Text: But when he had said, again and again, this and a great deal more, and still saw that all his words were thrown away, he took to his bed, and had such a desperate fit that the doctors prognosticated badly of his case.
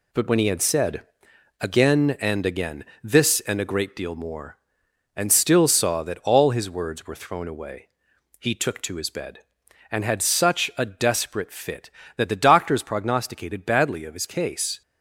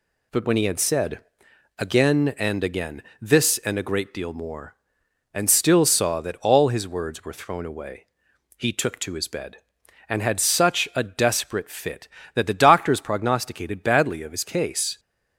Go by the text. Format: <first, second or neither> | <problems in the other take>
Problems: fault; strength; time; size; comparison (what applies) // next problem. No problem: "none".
second | gets quieter; noticeable; throughout; 6 dB